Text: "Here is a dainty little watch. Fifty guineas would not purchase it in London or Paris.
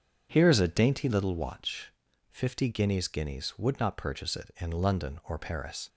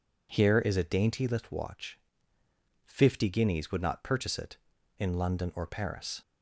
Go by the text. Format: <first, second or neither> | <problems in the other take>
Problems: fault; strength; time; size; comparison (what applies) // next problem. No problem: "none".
second | says "guineas" twice; at 3.0 s